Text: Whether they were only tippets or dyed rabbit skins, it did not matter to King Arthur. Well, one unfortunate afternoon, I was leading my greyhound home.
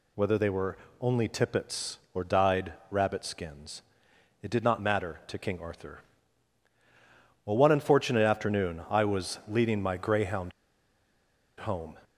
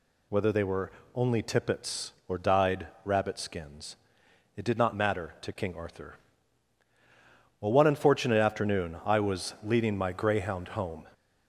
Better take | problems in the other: second | pauses between "were" and "only"; slight; at 0.7 s; 0.22 s long; slight in the second // pauses between "dyed" and "rabbit"; slight; at 2.7 s; 0.18 s long; slight in the second // pauses between "greyhound" and "home"; at 10.5 s; 1.0 s long

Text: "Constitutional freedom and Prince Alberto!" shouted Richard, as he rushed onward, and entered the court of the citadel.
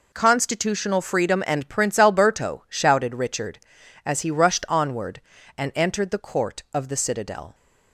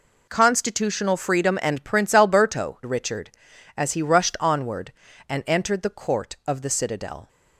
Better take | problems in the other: first | skips "shouted"; at 2.8 s

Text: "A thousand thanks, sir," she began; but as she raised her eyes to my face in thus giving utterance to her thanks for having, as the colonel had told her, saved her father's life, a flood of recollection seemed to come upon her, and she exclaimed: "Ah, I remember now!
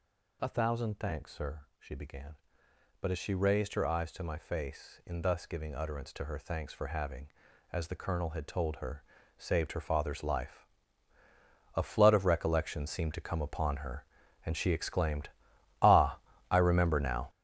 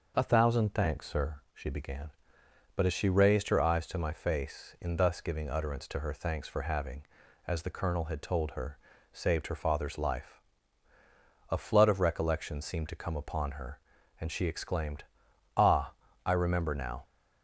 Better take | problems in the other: second | gets louder; strong; throughout; 10 dB

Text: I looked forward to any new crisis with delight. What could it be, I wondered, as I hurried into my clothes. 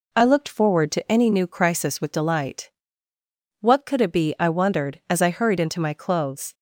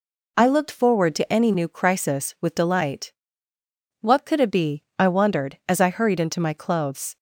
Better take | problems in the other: neither | none

